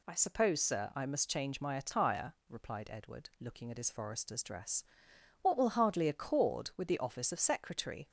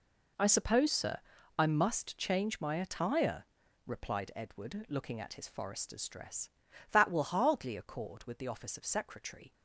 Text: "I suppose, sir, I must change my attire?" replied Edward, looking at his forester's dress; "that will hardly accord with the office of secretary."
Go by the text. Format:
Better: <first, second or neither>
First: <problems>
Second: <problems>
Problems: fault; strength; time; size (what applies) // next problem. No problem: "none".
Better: second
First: says "what" for "that"; at 5.4 s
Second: none